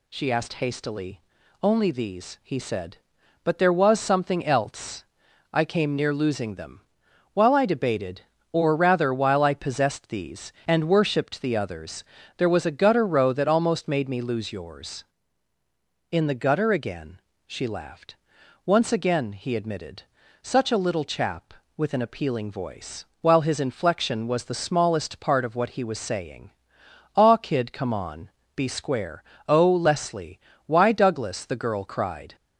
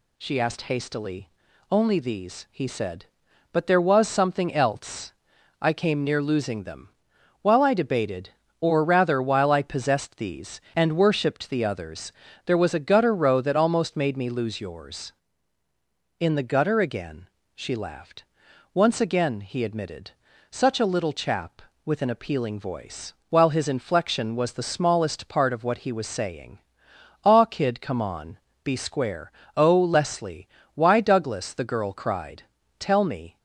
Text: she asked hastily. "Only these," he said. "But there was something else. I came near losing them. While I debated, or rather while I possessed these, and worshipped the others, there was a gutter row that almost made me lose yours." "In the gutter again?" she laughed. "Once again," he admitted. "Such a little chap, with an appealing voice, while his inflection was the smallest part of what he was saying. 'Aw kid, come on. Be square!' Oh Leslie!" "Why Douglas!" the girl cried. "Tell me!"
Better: second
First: stops before "Tell me"; at 32.3 s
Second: none

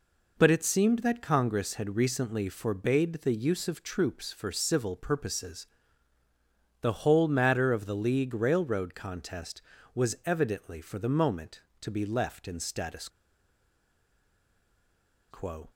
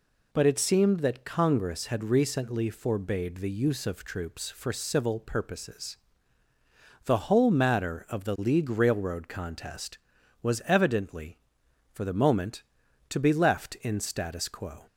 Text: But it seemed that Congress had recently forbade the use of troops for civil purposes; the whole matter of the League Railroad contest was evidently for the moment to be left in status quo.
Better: second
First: pauses between "status" and "quo"; strong; at 13.0 s; 2.2 s long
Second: none

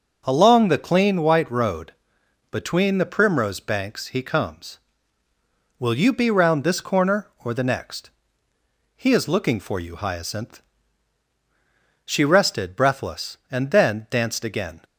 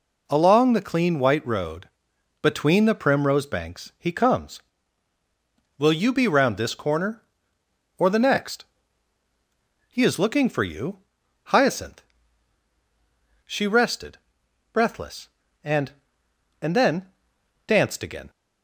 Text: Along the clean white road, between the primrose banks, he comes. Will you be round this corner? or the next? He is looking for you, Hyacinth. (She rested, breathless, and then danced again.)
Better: first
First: none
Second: says "and" twice; at 16.5 s // pauses between "then" and "danced"; noticeable; at 17.0 s; 0.60 s long

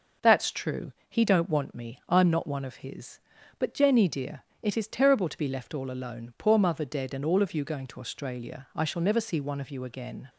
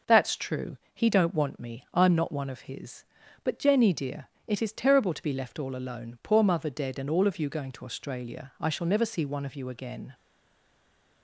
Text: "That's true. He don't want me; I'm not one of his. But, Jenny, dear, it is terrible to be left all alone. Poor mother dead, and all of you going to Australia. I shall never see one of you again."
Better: first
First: none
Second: stays silent after the last word; from 10.1 s on; 1.1 s long

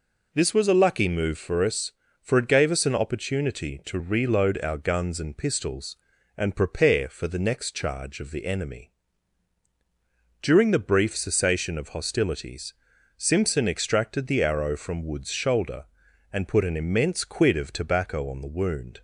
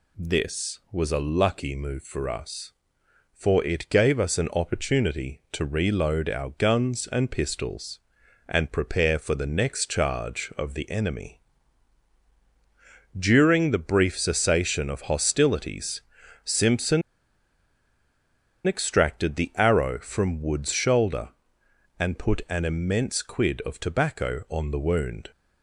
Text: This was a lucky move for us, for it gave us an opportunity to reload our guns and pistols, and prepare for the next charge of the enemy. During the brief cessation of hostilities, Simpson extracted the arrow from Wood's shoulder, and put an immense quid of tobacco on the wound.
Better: first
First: none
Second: pauses between "Simpson" and "extracted"; strong; at 17.0 s; 1.6 s long

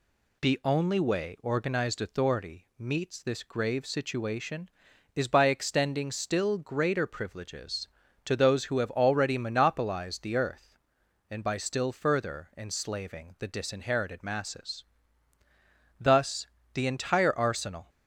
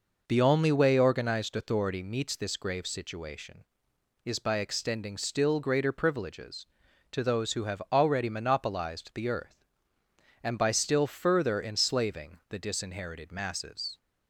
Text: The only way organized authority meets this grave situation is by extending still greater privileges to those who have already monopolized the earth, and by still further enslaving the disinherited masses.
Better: second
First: goes on to say "Thus the entire arsenal"; strong; from 15.9 s on; 1.9 s long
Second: none

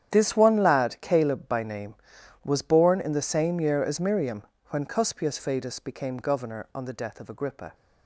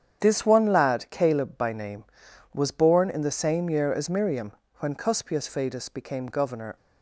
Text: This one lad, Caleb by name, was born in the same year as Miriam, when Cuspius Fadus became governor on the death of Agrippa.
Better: first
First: starts louder than the rest; strong; until 1.1 s; 9.5 dB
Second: starts louder than the rest; strong; until 1.2 s; 8.5 dB // stops before "on the death of Agrippa"; at 6.7 s

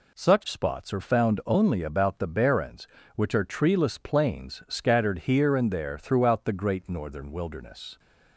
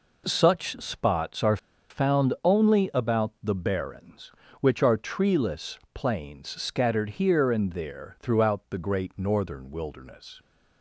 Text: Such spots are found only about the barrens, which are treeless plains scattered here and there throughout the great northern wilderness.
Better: first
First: none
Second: pauses between "are" and "found"; slight; at 1.5 s; 0.33 s long // pauses between "treeless" and "plains"; slight; at 5.7 s; 0.16 s long

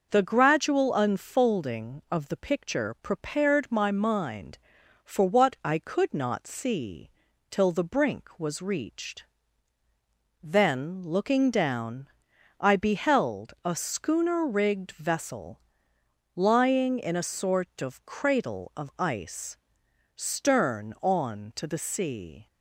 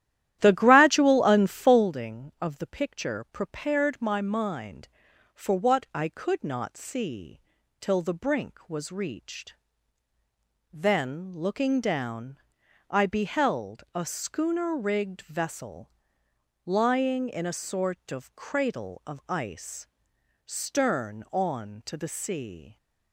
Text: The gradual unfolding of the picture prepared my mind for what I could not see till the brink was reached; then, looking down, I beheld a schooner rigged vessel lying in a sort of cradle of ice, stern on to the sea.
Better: first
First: pauses between "see" and "till"; at 7.1 s; 0.40 s long // pauses between "vessel" and "lying"; noticeable; at 15.6 s; 0.74 s long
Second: starts louder than the rest; strong; until 1.9 s; 12.5 dB // pauses between "see" and "till"; at 7.4 s; 0.40 s long // pauses between "vessel" and "lying"; noticeable; at 15.9 s; 0.74 s long

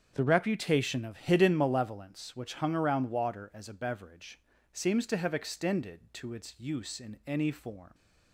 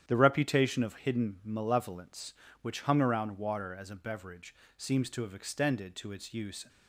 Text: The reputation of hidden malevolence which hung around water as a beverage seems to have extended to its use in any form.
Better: first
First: starts louder than the rest; until 1.1 s; 7 dB // pauses between "beverage" and "seems"; slight; at 4.3 s; 0.34 s long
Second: starts louder than the rest; strong; until 1.0 s; 9.5 dB // pauses between "beverage" and "seems"; slight; at 4.5 s; 0.24 s long // stops before "in any form"; at 6.6 s

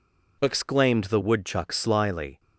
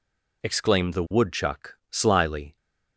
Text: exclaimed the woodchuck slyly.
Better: neither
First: none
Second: none

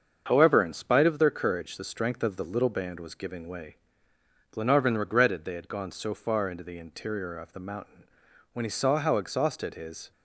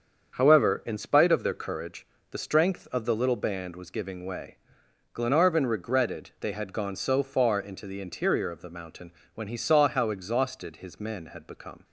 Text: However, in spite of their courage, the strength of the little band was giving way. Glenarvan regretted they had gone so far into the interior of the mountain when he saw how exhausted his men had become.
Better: second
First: starts louder than the rest; until 1.2 s; 7 dB // pauses between "mountain" and "when"; noticeable; at 8.0 s; 0.50 s long // stops before "men had become"; at 10.1 s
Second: starts louder than the rest; strong; until 1.3 s; 7 dB // pauses between "mountain" and "when"; slight; at 9.1 s; 0.24 s long

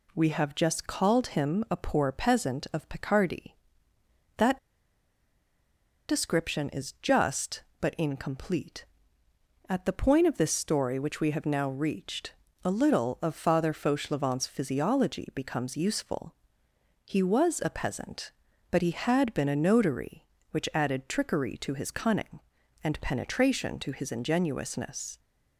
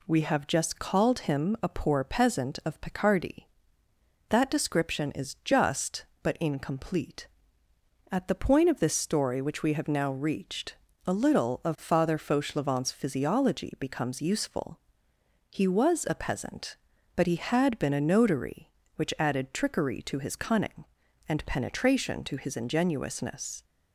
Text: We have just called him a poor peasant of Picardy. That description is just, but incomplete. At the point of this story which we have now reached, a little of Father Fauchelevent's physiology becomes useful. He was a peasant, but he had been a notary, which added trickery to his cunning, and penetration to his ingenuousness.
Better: second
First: pauses between "That" and "description"; strong; at 4.5 s; 1.5 s long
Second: none

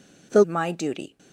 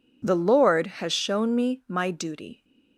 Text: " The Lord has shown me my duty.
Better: second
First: skips "Lord has shown me"; at 0.4 s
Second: none

